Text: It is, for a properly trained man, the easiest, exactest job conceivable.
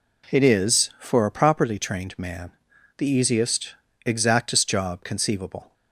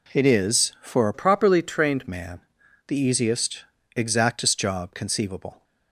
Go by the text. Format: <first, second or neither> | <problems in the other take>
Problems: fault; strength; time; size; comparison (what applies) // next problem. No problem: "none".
first | changes voice from "properly" to "trained"; from 1.1 to 2.0 s; 0.9 s long